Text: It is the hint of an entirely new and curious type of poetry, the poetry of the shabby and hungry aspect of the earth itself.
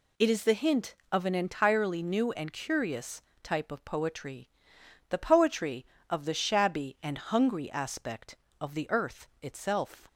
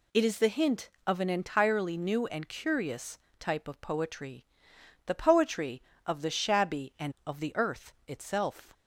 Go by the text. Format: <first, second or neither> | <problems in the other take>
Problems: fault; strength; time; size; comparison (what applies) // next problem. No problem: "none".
first | pauses between "curious" and "type"; slight; at 3.1 s; 0.18 s long; slight in the first // skips "hungry aspect"; at 7.1 s // pauses between "earth" and "itself"; slight; at 7.9 s; 0.16 s long; slight in the first